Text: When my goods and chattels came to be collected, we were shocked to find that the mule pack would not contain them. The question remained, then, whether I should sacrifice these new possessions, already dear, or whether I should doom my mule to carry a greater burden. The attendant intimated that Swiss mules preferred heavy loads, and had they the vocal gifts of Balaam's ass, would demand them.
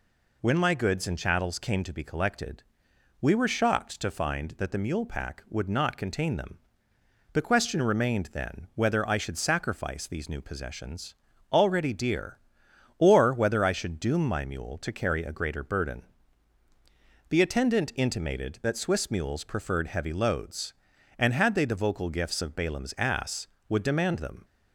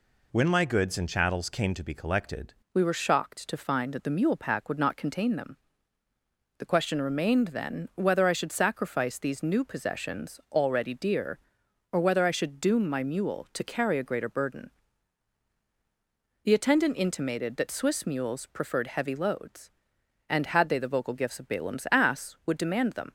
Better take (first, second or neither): first